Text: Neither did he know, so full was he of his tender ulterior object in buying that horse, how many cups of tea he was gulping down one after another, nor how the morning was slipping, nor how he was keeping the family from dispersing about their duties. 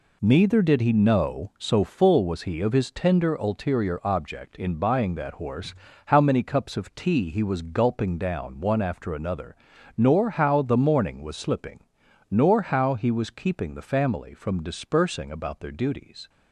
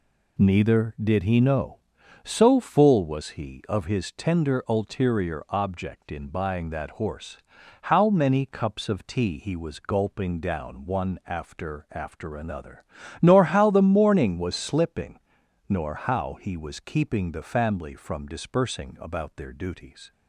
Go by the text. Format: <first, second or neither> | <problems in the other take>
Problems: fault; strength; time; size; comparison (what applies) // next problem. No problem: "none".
first | says "after" twice; at 11.8 s